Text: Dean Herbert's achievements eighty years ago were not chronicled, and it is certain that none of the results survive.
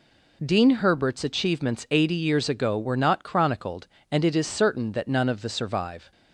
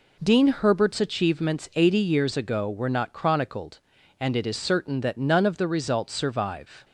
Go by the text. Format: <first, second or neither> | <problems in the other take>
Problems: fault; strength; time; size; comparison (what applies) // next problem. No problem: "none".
second | skips "results"; at 5.4 s